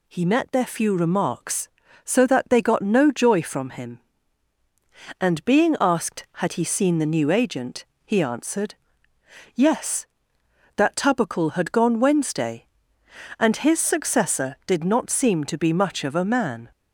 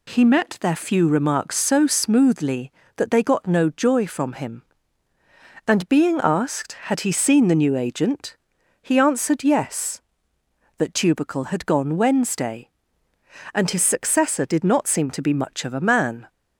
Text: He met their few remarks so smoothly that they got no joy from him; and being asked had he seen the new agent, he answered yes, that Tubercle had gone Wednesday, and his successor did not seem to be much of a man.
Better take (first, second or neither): second